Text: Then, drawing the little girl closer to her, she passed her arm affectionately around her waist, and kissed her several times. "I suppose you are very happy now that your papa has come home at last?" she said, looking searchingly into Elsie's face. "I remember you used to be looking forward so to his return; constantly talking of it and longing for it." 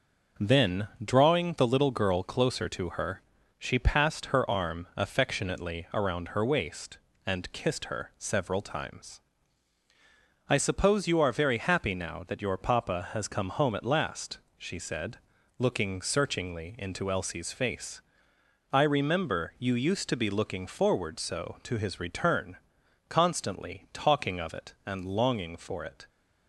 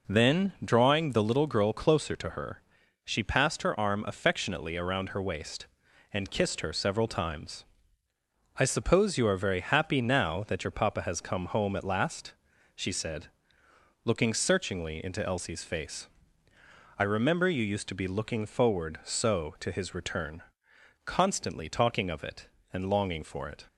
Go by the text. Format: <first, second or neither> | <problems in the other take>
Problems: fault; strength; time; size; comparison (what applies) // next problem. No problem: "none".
neither | none